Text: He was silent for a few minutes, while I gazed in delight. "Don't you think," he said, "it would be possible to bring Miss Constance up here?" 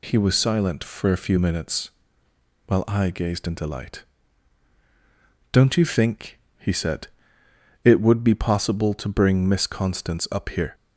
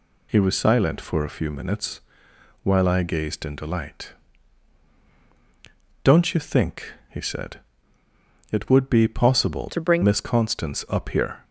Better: first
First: none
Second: changes voice from "to" to "bring"; from 9.6 to 10.0 s; 0.4 s long

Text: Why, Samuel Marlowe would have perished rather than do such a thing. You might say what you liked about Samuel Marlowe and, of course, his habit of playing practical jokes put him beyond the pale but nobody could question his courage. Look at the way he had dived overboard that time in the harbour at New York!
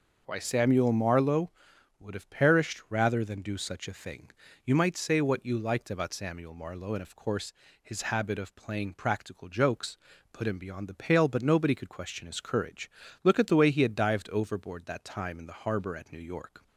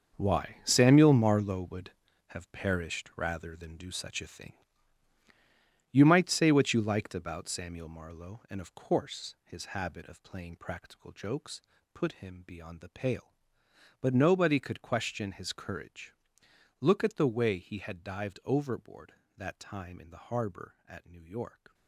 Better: first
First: pauses between "jokes" and "put"; slight; at 9.9 s; 0.36 s long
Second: gets quieter; strong; throughout; 11.5 dB // pauses between "jokes" and "put"; slight; at 11.6 s; 0.32 s long

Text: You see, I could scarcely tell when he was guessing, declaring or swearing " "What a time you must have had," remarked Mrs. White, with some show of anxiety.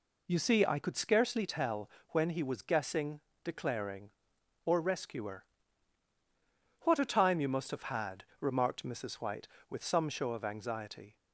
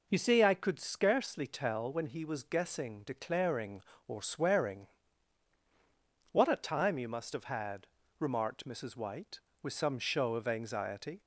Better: second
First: pauses between "tell" and "when"; slight; at 1.8 s; 0.20 s long // says "rescuer" for "swearing"; at 4.7 s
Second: none

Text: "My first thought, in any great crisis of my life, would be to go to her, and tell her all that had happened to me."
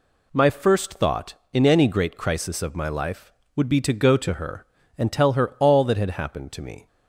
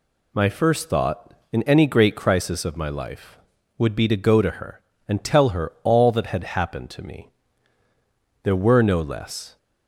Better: first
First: none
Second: goes on to say "There were no less"; noticeable; from 8.4 s on; 1.1 s long

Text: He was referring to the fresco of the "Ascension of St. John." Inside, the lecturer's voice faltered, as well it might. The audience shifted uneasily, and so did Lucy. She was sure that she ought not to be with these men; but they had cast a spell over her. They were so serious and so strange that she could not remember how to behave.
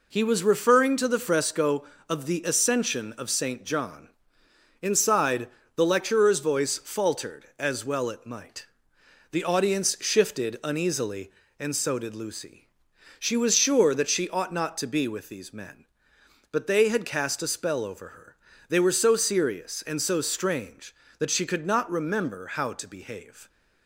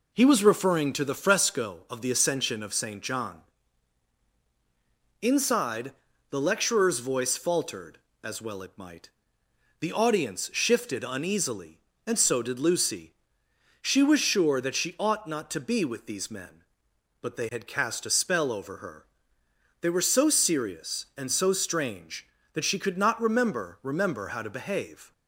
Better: first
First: none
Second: says "remember" twice; at 23.8 s

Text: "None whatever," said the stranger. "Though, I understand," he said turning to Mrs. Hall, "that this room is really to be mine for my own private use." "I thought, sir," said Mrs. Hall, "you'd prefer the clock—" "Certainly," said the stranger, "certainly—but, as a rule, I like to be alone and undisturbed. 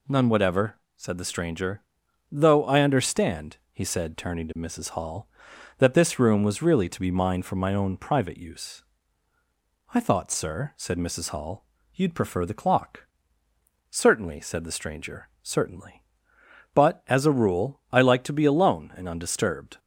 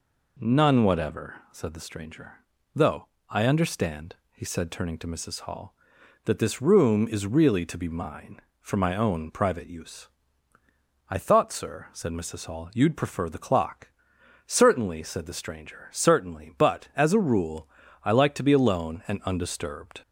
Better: second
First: says "was" for "is"; at 6.4 s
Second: none

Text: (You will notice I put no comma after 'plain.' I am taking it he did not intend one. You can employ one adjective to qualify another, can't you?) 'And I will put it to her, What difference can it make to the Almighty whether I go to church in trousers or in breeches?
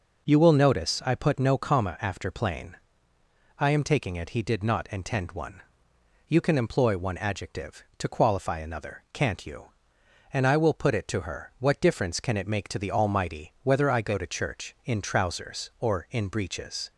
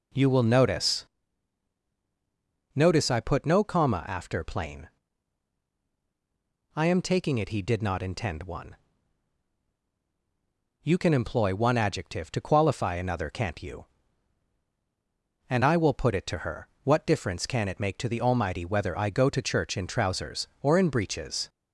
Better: first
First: none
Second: says "notice" twice; at 2.7 s

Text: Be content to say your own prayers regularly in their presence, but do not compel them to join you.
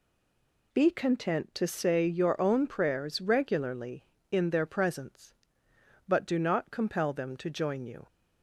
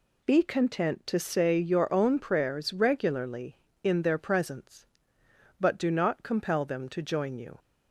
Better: second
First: stays silent before the first word; slight; until 0.7 s; 0.7 s long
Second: none

